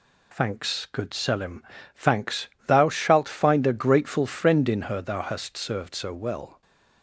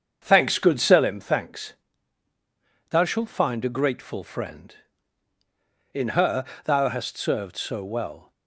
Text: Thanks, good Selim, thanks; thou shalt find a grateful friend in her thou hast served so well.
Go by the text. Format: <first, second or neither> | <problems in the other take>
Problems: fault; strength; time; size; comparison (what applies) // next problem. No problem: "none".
first | starts louder than the rest; strong; until 1.2 s; 7 dB // pauses between "her" and "thou"; slight; at 6.4 s; 0.18 s long